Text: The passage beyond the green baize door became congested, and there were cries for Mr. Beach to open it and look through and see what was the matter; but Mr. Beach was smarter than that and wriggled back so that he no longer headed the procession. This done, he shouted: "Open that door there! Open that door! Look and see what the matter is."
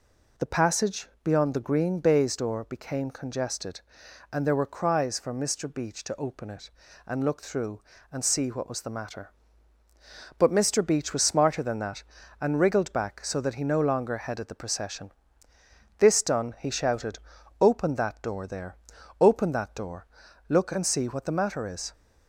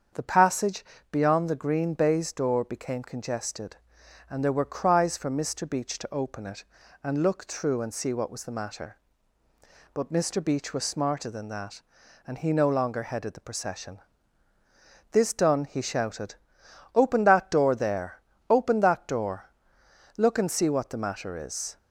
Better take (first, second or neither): first